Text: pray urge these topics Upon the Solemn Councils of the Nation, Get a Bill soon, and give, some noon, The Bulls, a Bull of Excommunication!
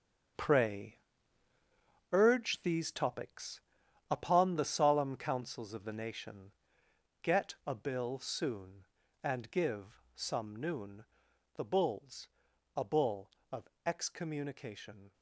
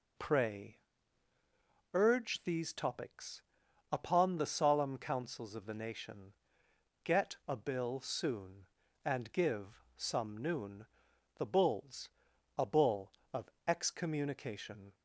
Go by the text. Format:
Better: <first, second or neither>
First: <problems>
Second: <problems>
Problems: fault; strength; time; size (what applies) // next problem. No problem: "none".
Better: second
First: gets quieter; strong; throughout; 11 dB // pauses between "pray" and "urge"; at 0.9 s; 1.1 s long // pauses between "topics" and "Upon"; noticeable; at 3.5 s; 0.52 s long // pauses between "of" and "Excommunication"; slight; at 13.6 s; 0.18 s long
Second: pauses between "pray" and "urge"; at 0.7 s; 1.1 s long // pauses between "topics" and "Upon"; noticeable; at 3.4 s; 0.52 s long // pauses between "of" and "Excommunication"; slight; at 13.5 s; 0.18 s long